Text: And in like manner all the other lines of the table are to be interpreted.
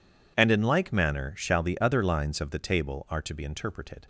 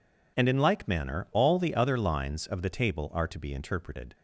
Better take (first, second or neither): second